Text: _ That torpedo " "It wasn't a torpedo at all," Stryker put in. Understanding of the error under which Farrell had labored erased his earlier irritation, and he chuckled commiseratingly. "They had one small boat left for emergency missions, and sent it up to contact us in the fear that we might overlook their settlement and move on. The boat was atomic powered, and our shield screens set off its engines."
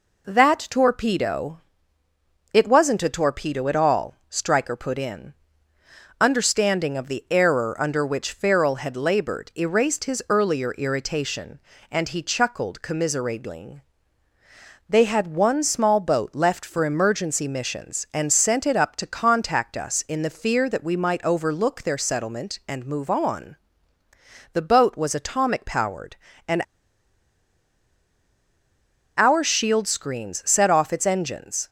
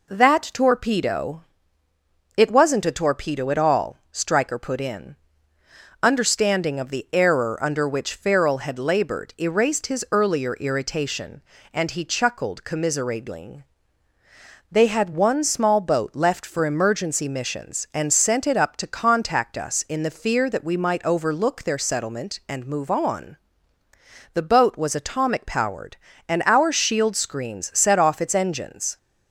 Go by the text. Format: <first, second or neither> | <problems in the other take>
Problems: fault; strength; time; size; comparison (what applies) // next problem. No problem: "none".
second | pauses between "and" and "our"; strong; at 26.6 s; 2.5 s long